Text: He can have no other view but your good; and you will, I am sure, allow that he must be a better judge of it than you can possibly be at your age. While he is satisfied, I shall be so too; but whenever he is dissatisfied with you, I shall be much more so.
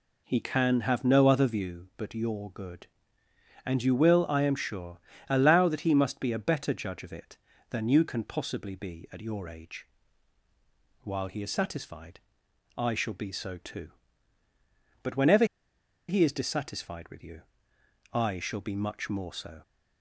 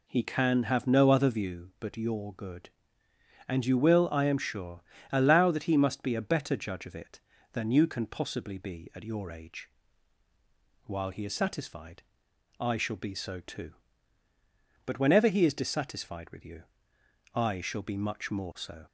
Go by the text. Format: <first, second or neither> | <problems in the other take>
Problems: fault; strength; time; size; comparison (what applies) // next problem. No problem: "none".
second | pauses between "whenever" and "he"; noticeable; at 15.4 s; 0.63 s long